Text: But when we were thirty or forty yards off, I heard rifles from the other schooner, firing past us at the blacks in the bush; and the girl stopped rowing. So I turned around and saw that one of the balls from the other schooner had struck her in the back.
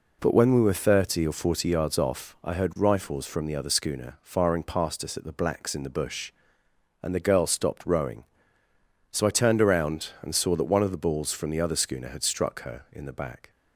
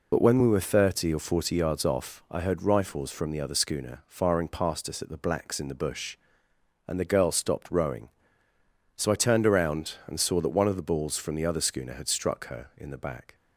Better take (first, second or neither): first